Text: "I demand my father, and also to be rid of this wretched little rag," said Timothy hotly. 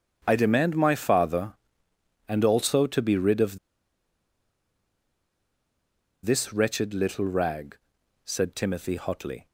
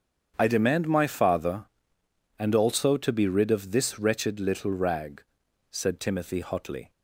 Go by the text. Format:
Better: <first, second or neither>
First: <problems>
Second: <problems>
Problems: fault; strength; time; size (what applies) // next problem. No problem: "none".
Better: second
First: starts louder than the rest; strong; until 1.2 s; 8 dB // pauses between "of" and "this"; strong; at 3.5 s; 2.6 s long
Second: starts louder than the rest; strong; until 1.3 s; 8 dB